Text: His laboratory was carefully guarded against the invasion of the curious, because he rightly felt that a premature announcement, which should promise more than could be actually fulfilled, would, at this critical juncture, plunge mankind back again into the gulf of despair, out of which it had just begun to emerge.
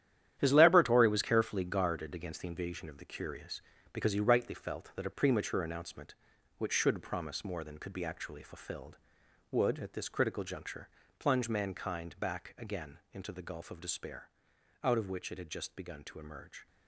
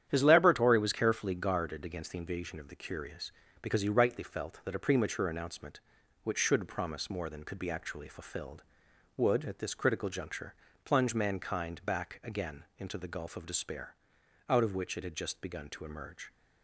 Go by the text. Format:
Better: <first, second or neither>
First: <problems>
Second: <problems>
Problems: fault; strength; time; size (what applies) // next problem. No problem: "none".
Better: second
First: gets quieter; strong; throughout; 10.5 dB // starts louder than the rest; strong; until 1.3 s; 10.5 dB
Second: starts louder than the rest; strong; until 1.1 s; 9.5 dB